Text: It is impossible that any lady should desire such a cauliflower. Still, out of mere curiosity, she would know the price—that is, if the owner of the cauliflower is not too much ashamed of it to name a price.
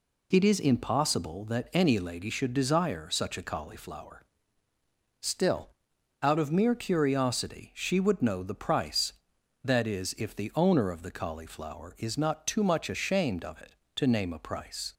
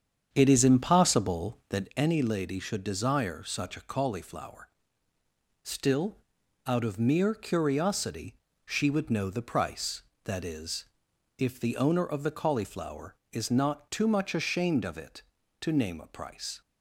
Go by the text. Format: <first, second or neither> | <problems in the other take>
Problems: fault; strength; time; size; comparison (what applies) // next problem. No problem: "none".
first | starts louder than the rest; strong; until 1.9 s; 8 dB